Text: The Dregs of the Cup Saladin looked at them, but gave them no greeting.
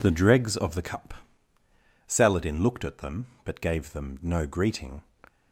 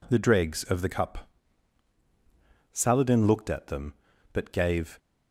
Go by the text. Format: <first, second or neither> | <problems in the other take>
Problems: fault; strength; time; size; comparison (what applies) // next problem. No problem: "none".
first | pauses between "Cup" and "Saladin"; strong; at 1.2 s; 1.4 s long; noticeable in the first // stops before "them no greeting"; at 4.9 s